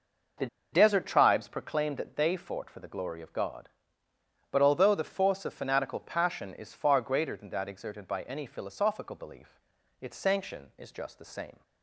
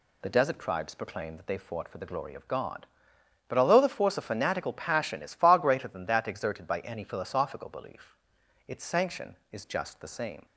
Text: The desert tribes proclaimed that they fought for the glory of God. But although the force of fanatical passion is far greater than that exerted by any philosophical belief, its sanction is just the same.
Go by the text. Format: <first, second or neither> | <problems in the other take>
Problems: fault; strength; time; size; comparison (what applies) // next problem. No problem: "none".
second | pauses between "The" and "desert"; slight; at 0.4 s; 0.25 s long